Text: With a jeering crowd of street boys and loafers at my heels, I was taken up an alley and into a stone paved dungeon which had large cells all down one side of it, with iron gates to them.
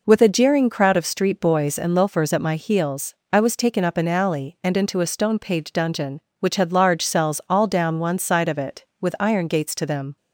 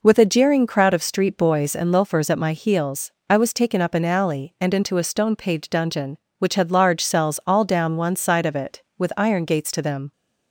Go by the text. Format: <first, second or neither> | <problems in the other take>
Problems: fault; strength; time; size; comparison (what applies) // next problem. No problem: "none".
neither | none